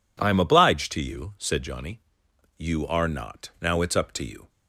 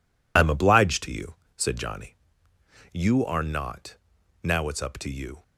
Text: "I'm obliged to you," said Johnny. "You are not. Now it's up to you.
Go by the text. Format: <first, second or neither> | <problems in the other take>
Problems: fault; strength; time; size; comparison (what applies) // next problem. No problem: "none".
first | loses the start of "I'm"; at 0.3 s; 40 ms